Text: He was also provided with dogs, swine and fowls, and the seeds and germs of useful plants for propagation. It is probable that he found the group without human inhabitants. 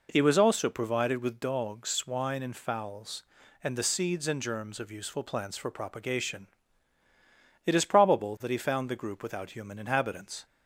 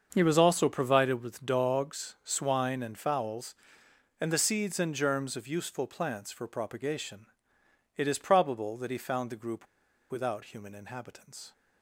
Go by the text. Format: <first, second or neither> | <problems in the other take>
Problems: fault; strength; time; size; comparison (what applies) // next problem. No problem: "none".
first | starts louder than the rest; until 1.1 s; 6.5 dB // pauses between "group" and "without"; at 9.6 s; 0.44 s long